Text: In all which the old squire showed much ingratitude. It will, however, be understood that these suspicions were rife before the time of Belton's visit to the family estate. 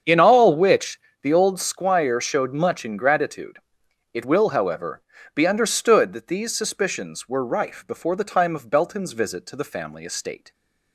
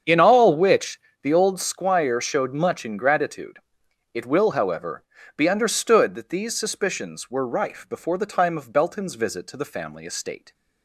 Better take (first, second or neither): neither